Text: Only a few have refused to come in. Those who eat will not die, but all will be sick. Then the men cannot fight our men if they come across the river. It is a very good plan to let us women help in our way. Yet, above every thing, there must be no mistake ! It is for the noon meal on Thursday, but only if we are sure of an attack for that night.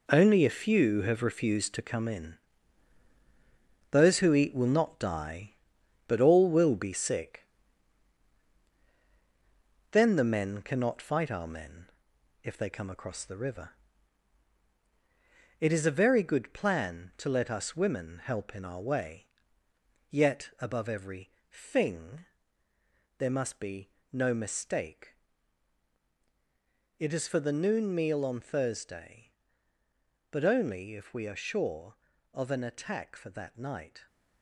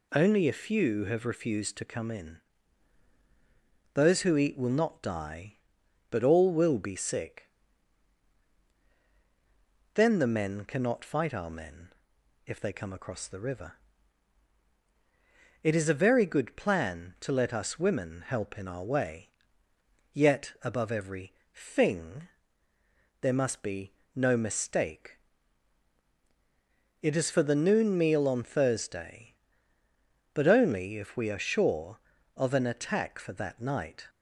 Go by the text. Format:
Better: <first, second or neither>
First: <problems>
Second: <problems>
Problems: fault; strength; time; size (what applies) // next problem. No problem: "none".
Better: second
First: gets quieter; strong; throughout; 9 dB // pauses between "men" and "if"; noticeable; at 11.8 s; 0.58 s long // pauses between "every" and "thing"; slight; at 21.2 s; 0.20 s long // pauses between "be" and "no"; slight; at 23.8 s; 0.24 s long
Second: pauses between "men" and "if"; noticeable; at 11.8 s; 0.58 s long // pauses between "every" and "thing"; slight; at 21.3 s; 0.20 s long // pauses between "be" and "no"; slight; at 23.9 s; 0.24 s long